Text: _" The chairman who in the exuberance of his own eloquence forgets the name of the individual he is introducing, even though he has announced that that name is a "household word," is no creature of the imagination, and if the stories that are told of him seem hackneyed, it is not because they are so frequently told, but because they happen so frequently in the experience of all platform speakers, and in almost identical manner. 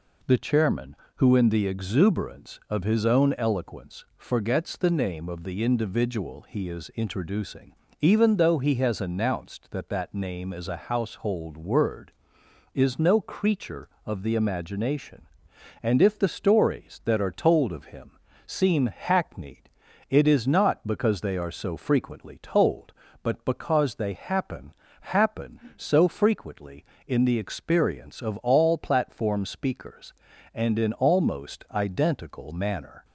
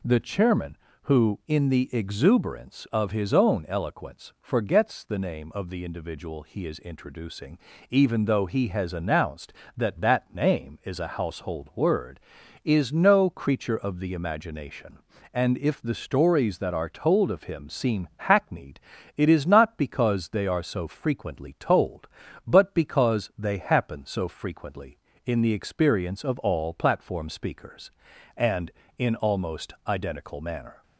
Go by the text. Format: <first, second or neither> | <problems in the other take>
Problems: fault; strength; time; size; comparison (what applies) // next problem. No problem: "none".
second | pauses between "him" and "seem"; slight; at 18.1 s; 0.34 s long // says "happen" twice; at 25.0 s